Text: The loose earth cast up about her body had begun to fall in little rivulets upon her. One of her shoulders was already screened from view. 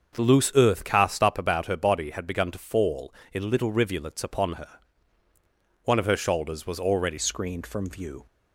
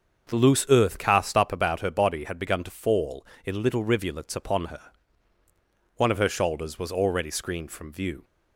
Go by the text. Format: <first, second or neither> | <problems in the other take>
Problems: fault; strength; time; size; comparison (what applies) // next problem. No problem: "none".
second | starts louder than the rest; until 1.1 s; 6.5 dB; also in the second // changes voice at "screened"; from 7.1 s on; 1.1 s long